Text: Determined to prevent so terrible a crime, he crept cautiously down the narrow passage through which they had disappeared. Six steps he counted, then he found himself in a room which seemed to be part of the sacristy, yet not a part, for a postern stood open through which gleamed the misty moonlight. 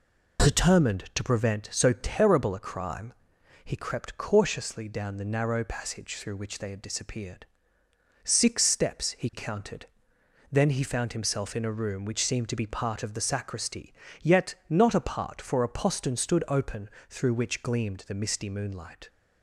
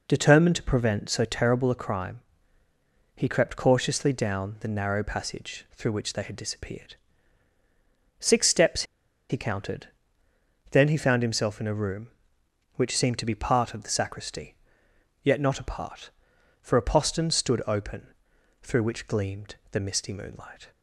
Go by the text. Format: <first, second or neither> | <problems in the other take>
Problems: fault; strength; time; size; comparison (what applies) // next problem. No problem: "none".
first | pauses between "steps" and "he"; noticeable; at 8.8 s; 0.46 s long // pauses between "open" and "through"; noticeable; at 18.0 s; 0.54 s long; slight in the first // pauses between "gleamed" and "the"; slight; at 19.5 s; 0.16 s long